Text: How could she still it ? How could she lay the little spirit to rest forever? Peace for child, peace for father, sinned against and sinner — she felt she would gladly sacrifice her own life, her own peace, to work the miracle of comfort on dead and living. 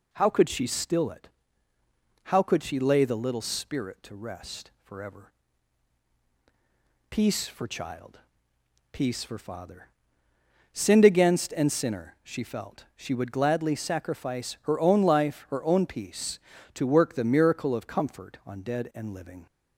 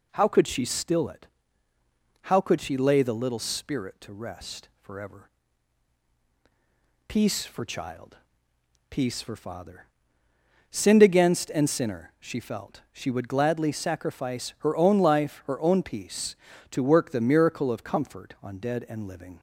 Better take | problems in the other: neither | none

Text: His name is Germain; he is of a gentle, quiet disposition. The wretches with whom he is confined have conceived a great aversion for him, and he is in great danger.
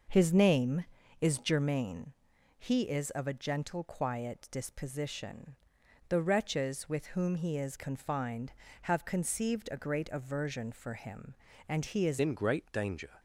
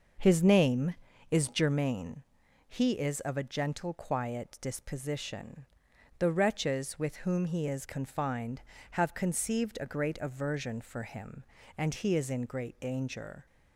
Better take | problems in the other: second | changes voice at "in"; from 12.1 s on; 1.0 s long

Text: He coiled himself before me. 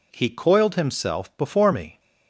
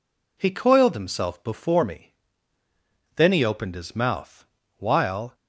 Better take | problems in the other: first | goes on to say "Then he opened his mouth while"; strong; from 3.1 s on; 2.2 s long

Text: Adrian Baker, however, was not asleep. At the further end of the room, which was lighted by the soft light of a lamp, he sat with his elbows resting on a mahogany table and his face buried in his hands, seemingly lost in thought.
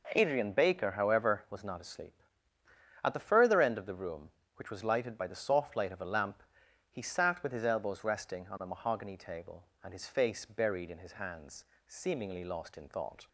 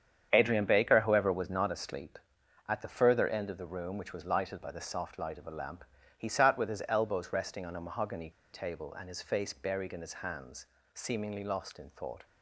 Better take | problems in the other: first | starts louder than the rest; strong; until 1.3 s; 8 dB // pauses between "mahogany" and "table"; slight; at 8.3 s; 0.22 s long

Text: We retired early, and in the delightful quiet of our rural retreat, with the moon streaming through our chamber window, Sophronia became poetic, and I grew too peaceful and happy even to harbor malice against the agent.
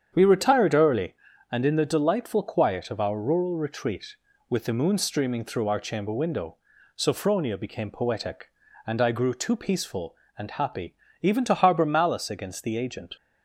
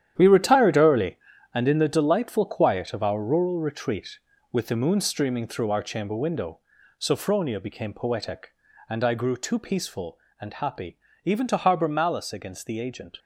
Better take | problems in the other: first | gets quieter; strong; throughout; 10.5 dB // starts louder than the rest; strong; until 1.1 s; 10 dB; strong in the first // pauses between "happy" and "even"; slight; at 10.9 s; 0.28 s long; slight in the first

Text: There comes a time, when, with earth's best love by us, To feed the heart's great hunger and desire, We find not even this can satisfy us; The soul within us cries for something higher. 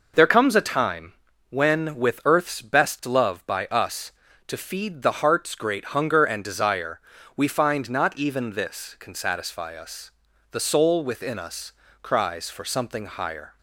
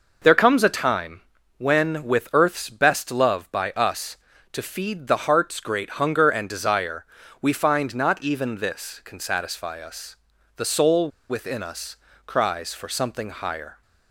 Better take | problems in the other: first | pauses between "soul" and "within"; slight; at 11.0 s; 0.20 s long // pauses between "us" and "cries"; slight; at 11.9 s; 0.30 s long; slight in the first

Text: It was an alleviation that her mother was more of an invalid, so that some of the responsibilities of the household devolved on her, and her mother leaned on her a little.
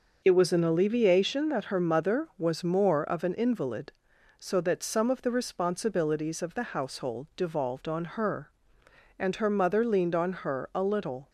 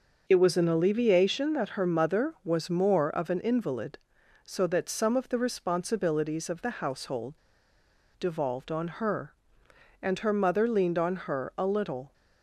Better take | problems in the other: first | starts louder than the rest; noticeable; until 1.2 s; 6 dB; noticeable in the first // pauses between "household" and "devolved"; noticeable; at 7.3 s; 0.86 s long

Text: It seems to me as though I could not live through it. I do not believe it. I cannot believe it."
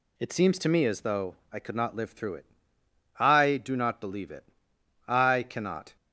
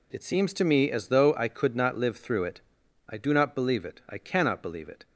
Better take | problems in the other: second | pauses between "though" and "I"; slight; at 1.3 s; 0.16 s long // stops before "believe it"; at 5.9 s

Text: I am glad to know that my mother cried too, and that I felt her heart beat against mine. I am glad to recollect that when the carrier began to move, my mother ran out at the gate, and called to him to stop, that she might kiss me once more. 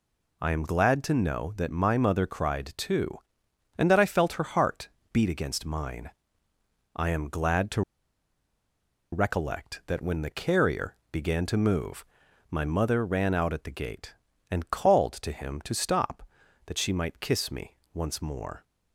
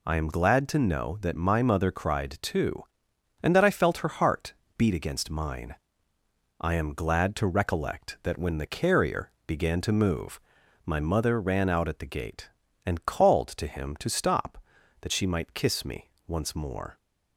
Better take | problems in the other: second | pauses between "heart" and "beat"; slight; at 4.8 s; 0.22 s long; slight in the second // pauses between "to" and "recollect"; strong; at 7.8 s; 1.3 s long // pauses between "carrier" and "began"; slight; at 10.9 s; 0.16 s long; slight in the second // pauses between "me" and "once"; slight; at 17.7 s; 0.18 s long; slight in the second

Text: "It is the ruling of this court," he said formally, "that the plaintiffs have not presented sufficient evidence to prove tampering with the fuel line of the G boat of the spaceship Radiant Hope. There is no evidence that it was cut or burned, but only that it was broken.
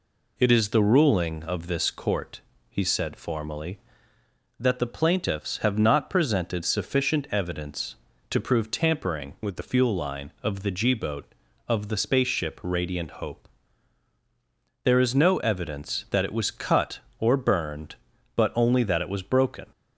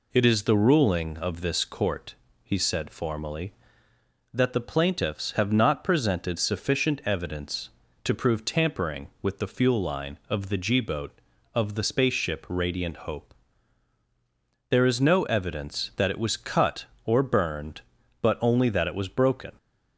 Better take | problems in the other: second | changes voice from "with" to "the"; from 9.4 to 9.6 s; 0.2 s long

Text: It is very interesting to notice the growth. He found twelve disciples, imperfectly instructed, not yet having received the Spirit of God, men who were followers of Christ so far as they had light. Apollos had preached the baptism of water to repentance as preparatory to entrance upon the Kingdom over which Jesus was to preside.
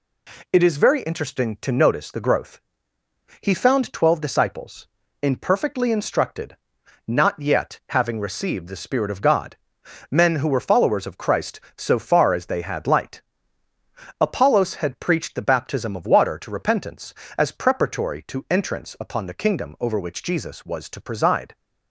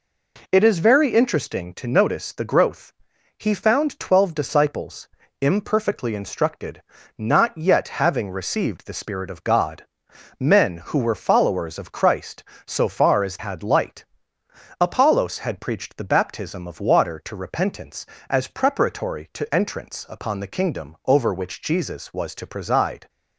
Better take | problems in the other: first | skips "they"; at 13.3 s

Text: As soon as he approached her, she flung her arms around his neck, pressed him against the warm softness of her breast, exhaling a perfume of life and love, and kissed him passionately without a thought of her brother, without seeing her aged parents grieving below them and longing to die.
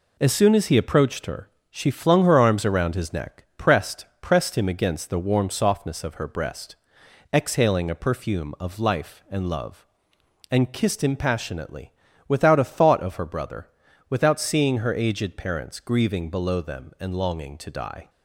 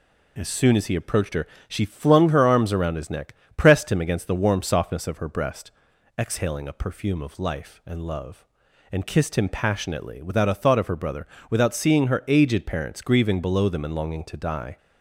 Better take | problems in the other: second | says "pressed" twice; at 4.1 s // pauses between "passionately" and "without"; slight; at 11.9 s; 0.34 s long

